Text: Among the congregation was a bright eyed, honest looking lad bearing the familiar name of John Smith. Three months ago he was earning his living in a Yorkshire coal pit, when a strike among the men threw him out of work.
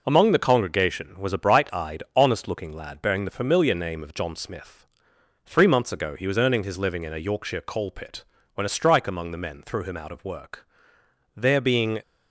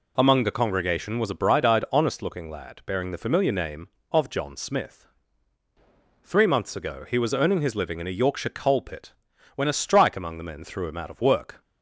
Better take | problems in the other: second | goes on to say "There being"; noticeable; from 11.3 s on; 0.64 s long

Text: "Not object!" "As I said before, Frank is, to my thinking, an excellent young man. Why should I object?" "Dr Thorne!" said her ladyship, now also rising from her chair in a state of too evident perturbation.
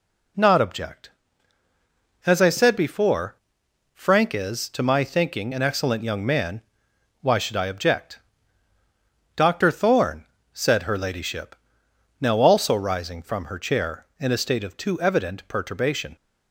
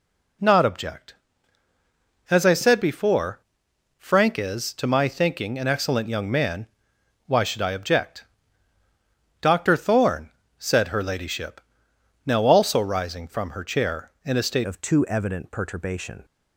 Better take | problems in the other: first | changes voice at "of"; from 14.6 s on; 1.6 s long

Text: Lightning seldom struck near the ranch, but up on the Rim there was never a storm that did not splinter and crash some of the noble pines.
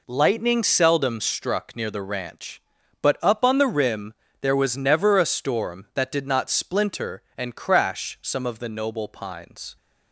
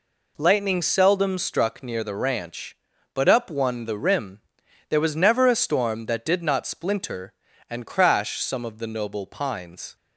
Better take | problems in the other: first | says "one" for "on"; at 3.4 s // pauses between "Rim" and "there"; noticeable; at 4.4 s; 0.48 s long; slight in the first

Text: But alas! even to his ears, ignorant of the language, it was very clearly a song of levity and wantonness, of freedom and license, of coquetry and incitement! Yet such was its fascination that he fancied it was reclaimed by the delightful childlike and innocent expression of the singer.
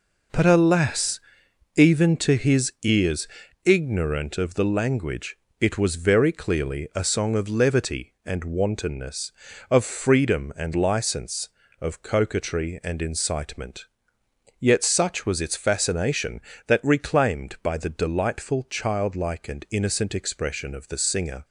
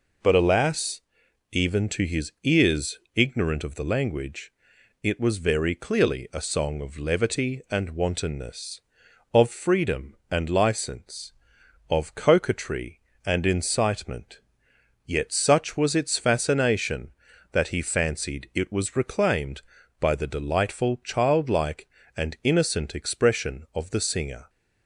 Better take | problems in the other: second | skips "he fancied it was"; at 16.8 s

